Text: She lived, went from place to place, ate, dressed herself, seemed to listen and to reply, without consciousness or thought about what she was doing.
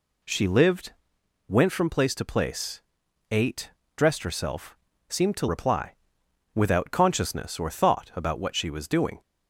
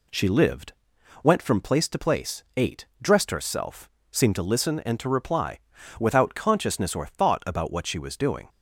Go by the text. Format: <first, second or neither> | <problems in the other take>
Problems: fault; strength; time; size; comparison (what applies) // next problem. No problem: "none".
second | skips "listen and to"; at 5.4 s